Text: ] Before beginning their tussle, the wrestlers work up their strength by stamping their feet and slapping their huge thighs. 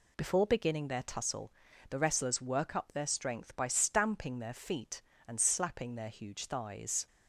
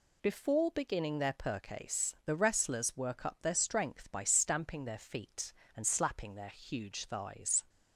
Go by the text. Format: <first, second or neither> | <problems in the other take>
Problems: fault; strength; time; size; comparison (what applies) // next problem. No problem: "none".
first | says "percase" for "tussle"; at 1.3 s